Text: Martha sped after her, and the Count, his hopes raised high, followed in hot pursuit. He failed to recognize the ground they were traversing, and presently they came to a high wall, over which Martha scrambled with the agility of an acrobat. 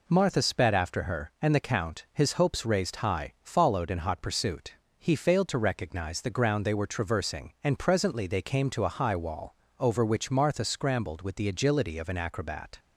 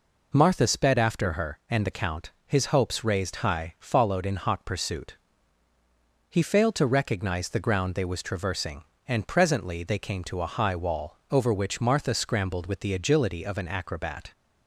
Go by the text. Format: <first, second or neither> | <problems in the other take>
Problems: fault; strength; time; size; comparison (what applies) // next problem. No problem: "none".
first | says "was" for "were"; at 8.0 s